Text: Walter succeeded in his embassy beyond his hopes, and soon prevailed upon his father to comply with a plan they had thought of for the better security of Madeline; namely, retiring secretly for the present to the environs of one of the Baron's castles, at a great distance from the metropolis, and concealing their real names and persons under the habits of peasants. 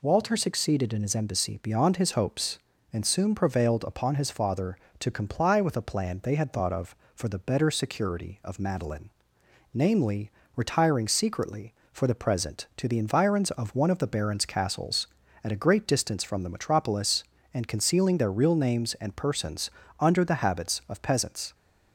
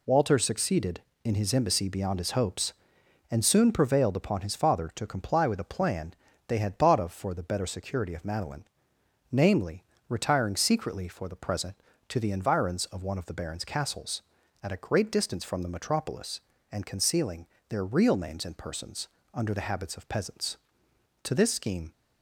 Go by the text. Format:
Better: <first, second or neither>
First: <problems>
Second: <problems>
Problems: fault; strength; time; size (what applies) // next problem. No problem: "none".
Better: first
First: pauses between "persons" and "under"; slight; at 19.7 s; 0.30 s long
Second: pauses between "plan" and "they"; slight; at 6.1 s; 0.34 s long // pauses between "concealing" and "their"; slight; at 17.4 s; 0.22 s long // pauses between "persons" and "under"; slight; at 19.0 s; 0.24 s long // goes on to say "To this scheme"; noticeable; from 21.2 s on; 0.68 s long